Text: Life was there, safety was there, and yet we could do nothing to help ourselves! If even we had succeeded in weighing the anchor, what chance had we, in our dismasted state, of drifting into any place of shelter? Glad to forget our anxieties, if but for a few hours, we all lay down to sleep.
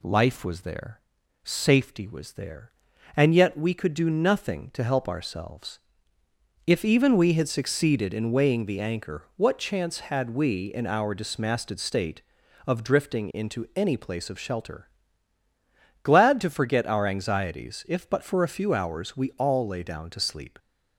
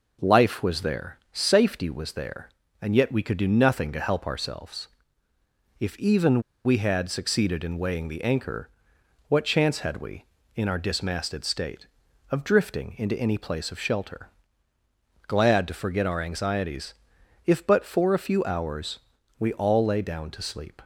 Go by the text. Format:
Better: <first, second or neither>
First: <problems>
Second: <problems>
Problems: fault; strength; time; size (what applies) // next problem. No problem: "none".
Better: first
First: none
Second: pauses between "even" and "we"; slight; at 6.4 s; 0.23 s long